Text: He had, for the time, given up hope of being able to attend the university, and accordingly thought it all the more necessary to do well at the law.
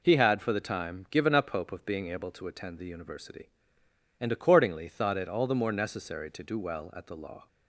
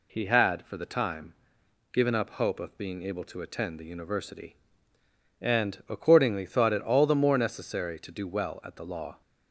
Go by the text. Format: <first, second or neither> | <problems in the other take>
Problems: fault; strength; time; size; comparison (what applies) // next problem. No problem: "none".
neither | none